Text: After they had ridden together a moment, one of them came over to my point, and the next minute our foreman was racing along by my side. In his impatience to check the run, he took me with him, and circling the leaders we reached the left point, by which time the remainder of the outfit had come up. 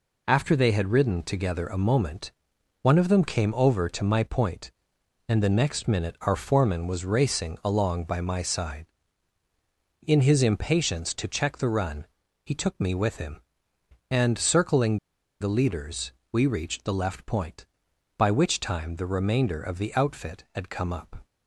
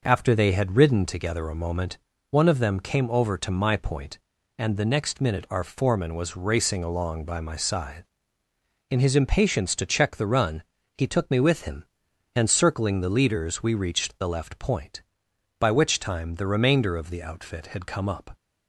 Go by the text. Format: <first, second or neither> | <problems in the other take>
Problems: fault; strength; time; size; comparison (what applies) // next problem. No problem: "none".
second | pauses between "circling" and "the"; at 14.9 s; 0.42 s long // pauses between "leaders" and "we"; slight; at 16.1 s; 0.20 s long